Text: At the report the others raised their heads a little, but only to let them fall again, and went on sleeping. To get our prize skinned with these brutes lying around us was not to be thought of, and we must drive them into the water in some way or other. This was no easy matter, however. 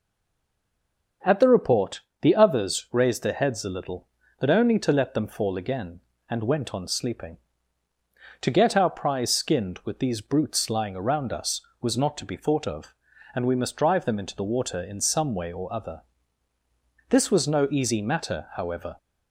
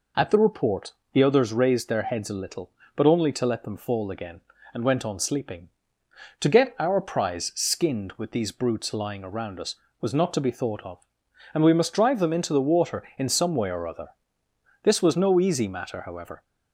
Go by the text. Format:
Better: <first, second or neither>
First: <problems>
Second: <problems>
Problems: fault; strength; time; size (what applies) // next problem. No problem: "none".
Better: second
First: stays silent before the first word; noticeable; until 1.2 s; 1.2 s long // starts louder than the rest; until 2.4 s; 6.5 dB // pauses between "report" and "the"; slight; at 2.0 s; 0.20 s long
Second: pauses between "report" and "the"; slight; at 0.9 s; 0.20 s long